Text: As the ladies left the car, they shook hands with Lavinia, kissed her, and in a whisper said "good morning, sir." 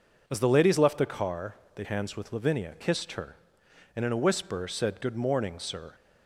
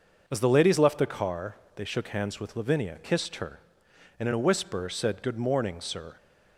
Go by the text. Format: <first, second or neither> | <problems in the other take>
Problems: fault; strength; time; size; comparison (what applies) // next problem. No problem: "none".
second | skips "shook"; at 1.8 s